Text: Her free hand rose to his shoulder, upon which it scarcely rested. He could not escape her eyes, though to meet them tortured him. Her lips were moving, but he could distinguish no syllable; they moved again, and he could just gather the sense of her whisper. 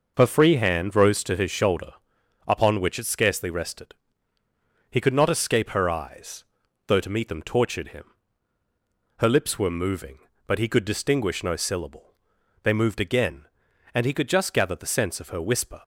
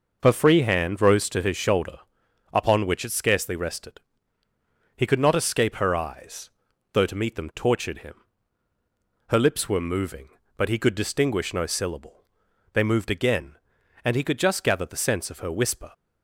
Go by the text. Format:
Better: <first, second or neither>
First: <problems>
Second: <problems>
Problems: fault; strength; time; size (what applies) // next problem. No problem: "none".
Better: neither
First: none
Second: none